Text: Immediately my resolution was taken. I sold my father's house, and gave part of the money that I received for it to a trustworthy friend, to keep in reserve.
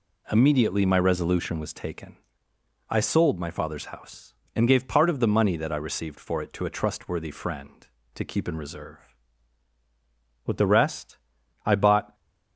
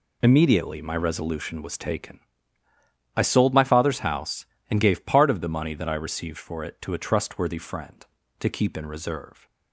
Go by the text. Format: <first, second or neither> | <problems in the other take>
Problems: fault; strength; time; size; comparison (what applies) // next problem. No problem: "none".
second | goes on to say "With the rest I bought"; strong; from 10.4 s on; 1.6 s long